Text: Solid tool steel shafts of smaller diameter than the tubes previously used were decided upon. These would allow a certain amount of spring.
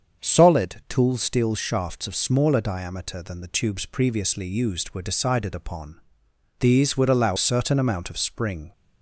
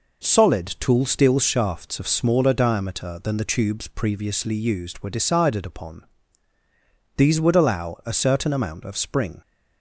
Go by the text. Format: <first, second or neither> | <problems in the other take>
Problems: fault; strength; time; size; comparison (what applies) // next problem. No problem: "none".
second | starts louder than the rest; until 1.2 s; 7 dB // skips "a"; at 7.3 s